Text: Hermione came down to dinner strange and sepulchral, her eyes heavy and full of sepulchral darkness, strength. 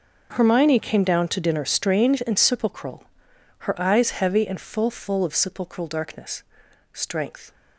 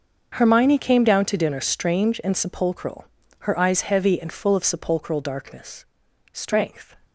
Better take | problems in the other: second | starts louder than the rest; until 1.3 s; 6.5 dB; also in the second // says "full" twice; at 4.8 s

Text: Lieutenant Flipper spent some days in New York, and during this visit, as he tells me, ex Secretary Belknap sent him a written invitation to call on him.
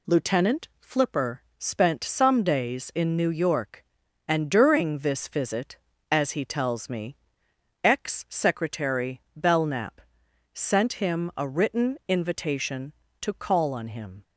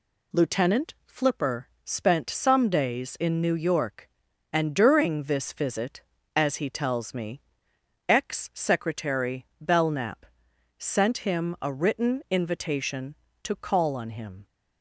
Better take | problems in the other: neither | pauses between "Flipper" and "spent"; slight; the same in both // pauses between "Belknap" and "sent"; noticeable; the same in both

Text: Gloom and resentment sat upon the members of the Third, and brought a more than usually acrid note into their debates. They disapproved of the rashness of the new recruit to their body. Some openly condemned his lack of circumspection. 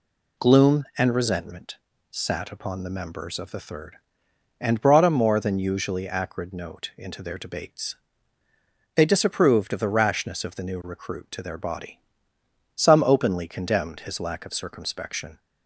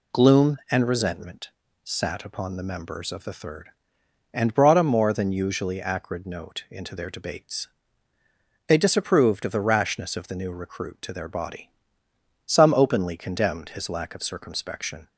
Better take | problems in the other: neither | pauses between "resentment" and "sat"; slight; the same in both

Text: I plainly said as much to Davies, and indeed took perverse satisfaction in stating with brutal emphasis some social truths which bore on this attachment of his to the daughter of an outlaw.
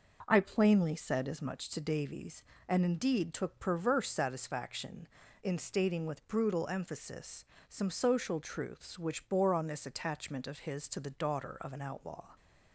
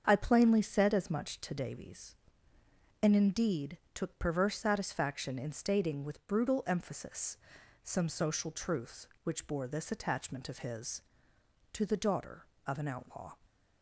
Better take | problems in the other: first | starts louder than the rest; strong; until 1.0 s; 7 dB // pauses between "indeed" and "took"; slight; at 3.7 s; 0.18 s long // pauses between "emphasis" and "some"; at 7.3 s; 0.44 s long; slight in the first // skips "on"; at 9.6 s

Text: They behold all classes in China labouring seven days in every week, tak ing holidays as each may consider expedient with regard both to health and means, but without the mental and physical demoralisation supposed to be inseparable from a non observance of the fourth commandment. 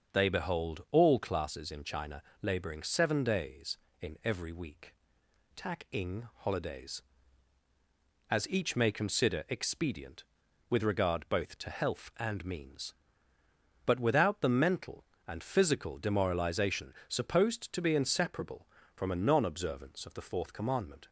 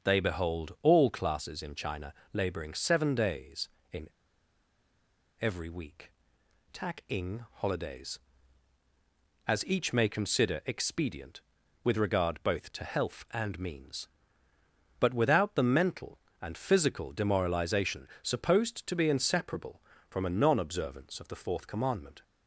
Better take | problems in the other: first | starts louder than the rest; until 1.0 s; 6.5 dB; also in the first // pauses between "China" and "labouring"; slight; at 2.1 s; 0.20 s long; slight in the first // pauses between "in" and "every"; strong; at 4.0 s; 1.3 s long

